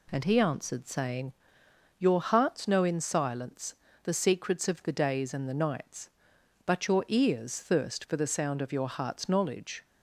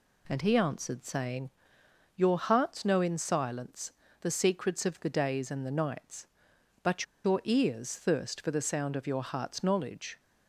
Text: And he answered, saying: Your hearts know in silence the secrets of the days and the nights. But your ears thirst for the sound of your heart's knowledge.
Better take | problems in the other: first | pauses between "silence" and "the"; slight; at 3.9 s; 0.30 s long; slight in the first // pauses between "But" and "your"; slight; at 7.0 s; 0.20 s long

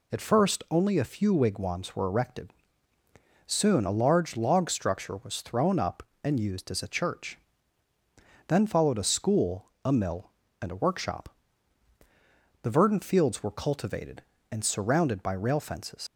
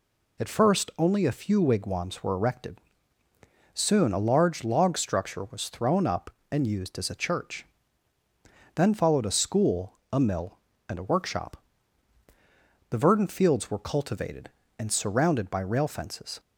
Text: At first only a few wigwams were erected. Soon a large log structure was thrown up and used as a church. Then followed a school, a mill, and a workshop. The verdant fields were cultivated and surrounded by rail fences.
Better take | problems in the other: second | leaves "fences" unfinished; at 16.0 s; 55 ms

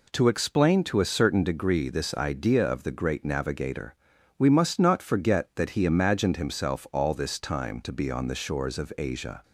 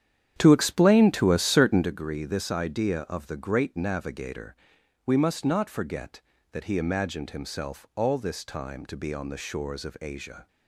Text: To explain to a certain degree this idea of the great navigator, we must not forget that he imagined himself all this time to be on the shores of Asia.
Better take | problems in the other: first | starts louder than the rest; strong; until 1.9 s; 9.5 dB

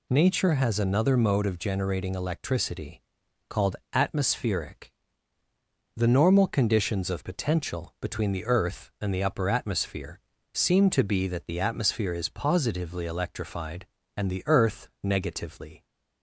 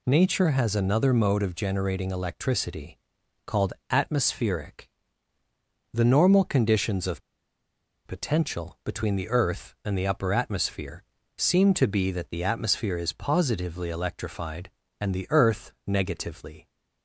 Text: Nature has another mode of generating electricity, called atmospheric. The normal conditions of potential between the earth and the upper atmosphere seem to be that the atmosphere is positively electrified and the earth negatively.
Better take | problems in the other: first | pauses between "called" and "atmospheric"; slight; at 3.7 s; 0.16 s long; slight in the first // pauses between "of" and "potential"; noticeable; at 7.2 s; 0.84 s long // pauses between "atmosphere" and "seem"; slight; at 11.0 s; 0.36 s long; slight in the first // pauses between "earth" and "negatively"; slight; at 15.7 s; 0.16 s long; slight in the first

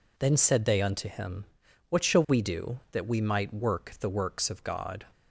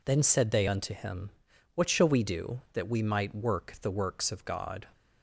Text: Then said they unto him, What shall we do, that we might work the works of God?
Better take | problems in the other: neither | none

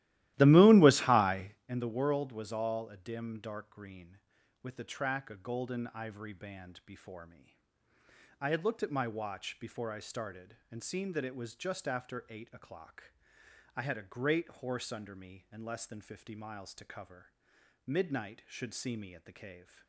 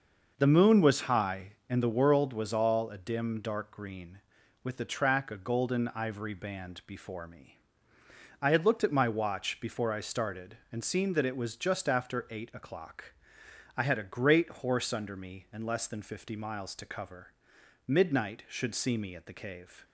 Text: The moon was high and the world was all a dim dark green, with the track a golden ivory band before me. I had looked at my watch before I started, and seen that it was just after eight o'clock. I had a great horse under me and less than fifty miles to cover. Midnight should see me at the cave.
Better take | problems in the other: second | starts louder than the rest; strong; until 1.6 s; 15.5 dB

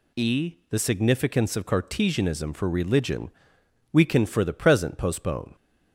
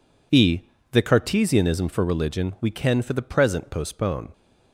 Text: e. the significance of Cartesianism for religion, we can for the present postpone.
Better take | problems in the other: first | skips "significance of"; at 1.0 s

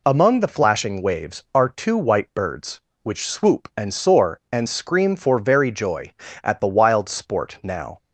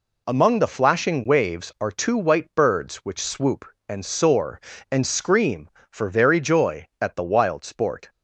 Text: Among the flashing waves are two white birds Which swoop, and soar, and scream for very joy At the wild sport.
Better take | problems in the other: second | goes on to say "Now"; slight; from 7.6 s on; 0.34 s long

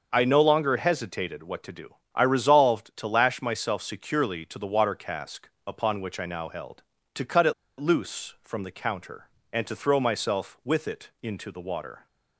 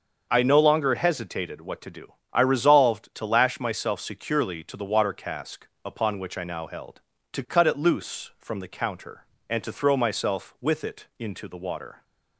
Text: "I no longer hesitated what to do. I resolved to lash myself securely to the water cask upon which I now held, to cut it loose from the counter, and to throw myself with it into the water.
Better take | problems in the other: second | starts louder than the rest; until 1.1 s; 6.5 dB; also in the second // pauses between "cask" and "upon"; slight; at 5.4 s; 0.16 s long; slight in the second // pauses between "it" and "loose"; slight; at 7.5 s; 0.27 s long

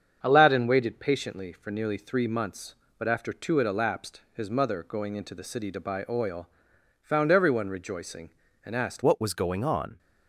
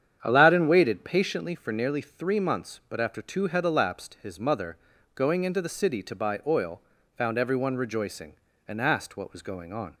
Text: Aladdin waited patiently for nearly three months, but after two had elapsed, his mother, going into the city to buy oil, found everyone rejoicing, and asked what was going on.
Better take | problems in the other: second | starts louder than the rest; strong; until 1.2 s; 7.5 dB; strong in the second // changes voice at "what"; from 9.0 s on; 0.9 s long

